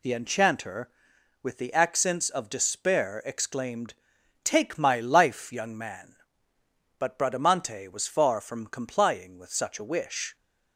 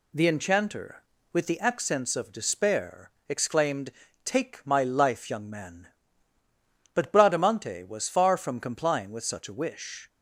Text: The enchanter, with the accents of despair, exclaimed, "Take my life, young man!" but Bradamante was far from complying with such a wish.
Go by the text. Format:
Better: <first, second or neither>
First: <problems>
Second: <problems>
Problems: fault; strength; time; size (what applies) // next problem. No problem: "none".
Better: neither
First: none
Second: none